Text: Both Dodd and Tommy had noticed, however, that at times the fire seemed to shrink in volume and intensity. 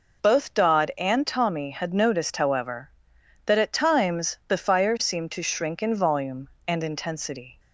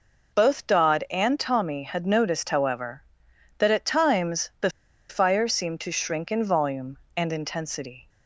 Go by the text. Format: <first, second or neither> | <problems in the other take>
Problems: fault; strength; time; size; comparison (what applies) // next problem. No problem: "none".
first | pauses between "the" and "fire"; at 4.6 s; 0.41 s long